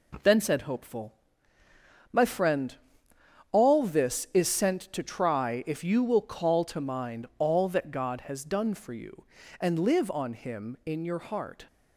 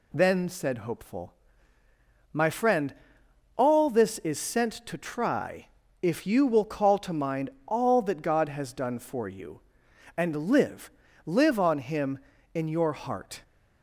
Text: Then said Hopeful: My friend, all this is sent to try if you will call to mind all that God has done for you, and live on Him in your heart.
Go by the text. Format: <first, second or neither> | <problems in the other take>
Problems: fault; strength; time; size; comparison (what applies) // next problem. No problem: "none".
first | pauses between "try" and "if"; slight; at 5.6 s; 0.34 s long // pauses between "mind" and "all"; slight; at 7.4 s; 0.18 s long // says "live" twice; at 11.2 s